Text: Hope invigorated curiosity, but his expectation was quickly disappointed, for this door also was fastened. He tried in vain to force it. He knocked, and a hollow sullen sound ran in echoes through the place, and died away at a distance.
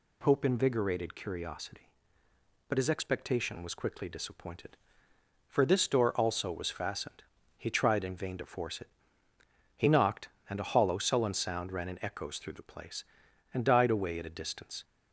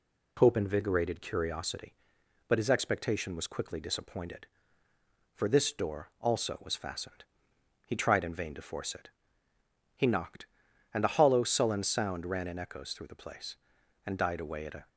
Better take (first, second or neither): first